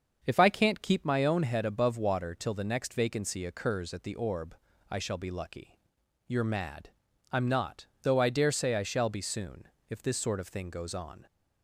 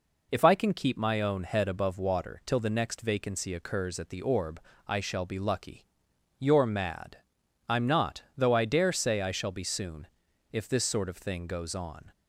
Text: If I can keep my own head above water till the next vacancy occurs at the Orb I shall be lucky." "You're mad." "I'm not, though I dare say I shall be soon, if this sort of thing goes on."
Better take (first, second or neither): second